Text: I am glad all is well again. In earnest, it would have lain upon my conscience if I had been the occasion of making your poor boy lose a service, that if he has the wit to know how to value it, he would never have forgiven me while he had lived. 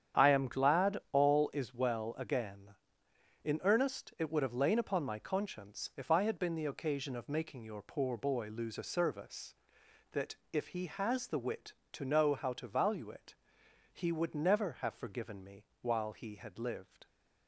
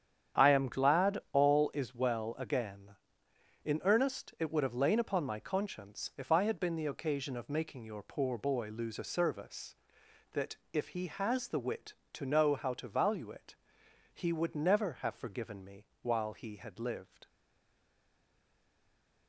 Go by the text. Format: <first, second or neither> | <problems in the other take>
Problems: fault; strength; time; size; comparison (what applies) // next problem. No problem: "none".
first | starts louder than the rest; strong; until 1.5 s; 9 dB; strong in the first // pauses between "that" and "if"; slight; at 10.5 s; 0.18 s long; slight in the first // pauses between "me" and "while"; slight; at 15.8 s; 0.16 s long; slight in the first // stays silent after the last word; noticeable; from 17.2 s on; 2.0 s long